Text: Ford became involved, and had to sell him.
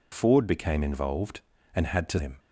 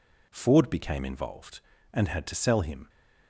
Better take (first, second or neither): second